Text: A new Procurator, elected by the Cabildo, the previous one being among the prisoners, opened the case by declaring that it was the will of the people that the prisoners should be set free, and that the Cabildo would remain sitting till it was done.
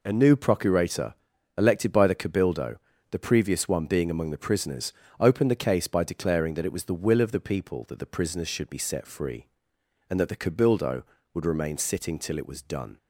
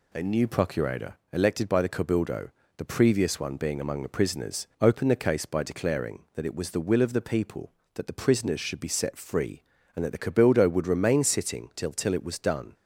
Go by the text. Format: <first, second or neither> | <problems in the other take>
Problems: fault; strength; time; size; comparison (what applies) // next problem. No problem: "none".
first | says "till" twice; at 11.9 s